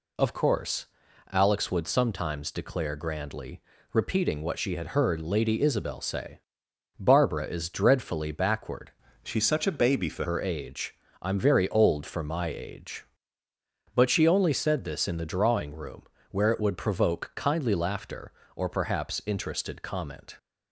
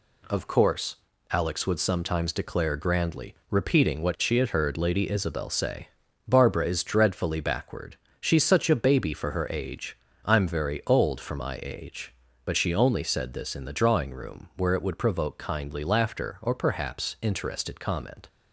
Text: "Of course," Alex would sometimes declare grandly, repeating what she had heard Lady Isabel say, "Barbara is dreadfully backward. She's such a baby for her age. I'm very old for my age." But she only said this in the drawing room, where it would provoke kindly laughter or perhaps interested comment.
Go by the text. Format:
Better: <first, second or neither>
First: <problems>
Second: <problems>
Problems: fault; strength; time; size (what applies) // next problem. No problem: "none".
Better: second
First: changes voice from "She's" to "for"; from 9.2 to 10.2 s; 1.0 s long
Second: none